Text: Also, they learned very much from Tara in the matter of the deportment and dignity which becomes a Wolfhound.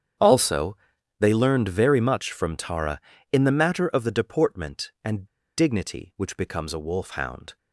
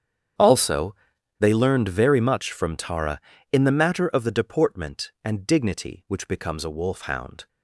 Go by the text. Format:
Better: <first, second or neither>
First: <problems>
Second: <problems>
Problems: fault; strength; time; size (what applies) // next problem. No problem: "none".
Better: second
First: starts louder than the rest; strong; until 1.6 s; 8.5 dB // pauses between "and" and "dignity"; slight; at 5.2 s; 0.31 s long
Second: starts louder than the rest; strong; until 1.8 s; 8.5 dB